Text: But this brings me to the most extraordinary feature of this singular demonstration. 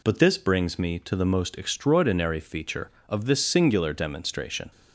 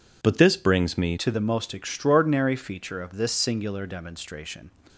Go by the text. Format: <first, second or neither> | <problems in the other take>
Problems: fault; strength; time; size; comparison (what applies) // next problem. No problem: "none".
first | changes voice at "to"; from 1.1 s on; 3.5 s long